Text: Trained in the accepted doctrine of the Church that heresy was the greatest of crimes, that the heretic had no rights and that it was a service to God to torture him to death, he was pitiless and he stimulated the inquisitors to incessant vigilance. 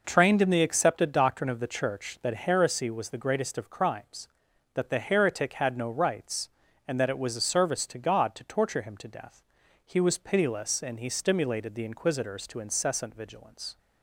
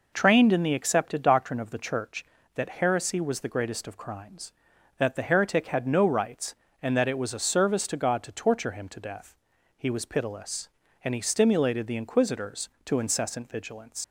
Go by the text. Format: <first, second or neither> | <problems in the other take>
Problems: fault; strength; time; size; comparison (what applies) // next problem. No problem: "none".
first | leaves "vigilance" unfinished; at 14.0 s; 90 ms